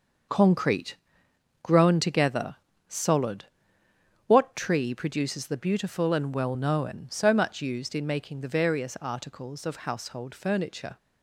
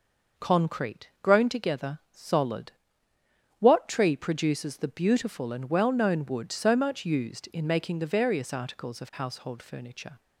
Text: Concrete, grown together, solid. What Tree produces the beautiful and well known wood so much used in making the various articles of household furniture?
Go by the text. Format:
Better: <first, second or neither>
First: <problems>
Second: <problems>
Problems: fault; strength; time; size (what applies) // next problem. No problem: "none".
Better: second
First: starts louder than the rest; noticeable; until 1.9 s; 6 dB // skips "wood"; at 7.0 s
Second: none